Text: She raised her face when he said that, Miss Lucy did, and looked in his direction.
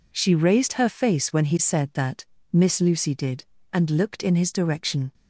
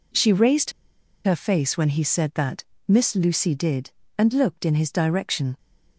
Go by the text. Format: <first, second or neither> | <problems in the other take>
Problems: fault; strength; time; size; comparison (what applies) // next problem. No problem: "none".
first | pauses between "raised" and "her"; noticeable; at 0.7 s; 0.53 s long